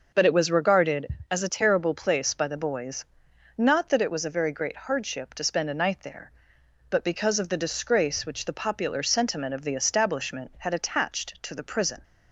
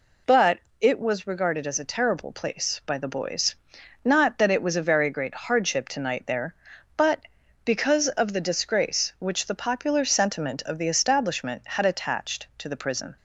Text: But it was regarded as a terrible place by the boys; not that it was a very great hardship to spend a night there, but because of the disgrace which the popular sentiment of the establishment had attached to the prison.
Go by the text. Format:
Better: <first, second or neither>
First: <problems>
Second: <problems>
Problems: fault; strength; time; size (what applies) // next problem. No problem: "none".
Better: first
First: none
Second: pauses between "But" and "it"; slight; at 0.5 s; 0.22 s long // skips "spend a"; at 6.0 s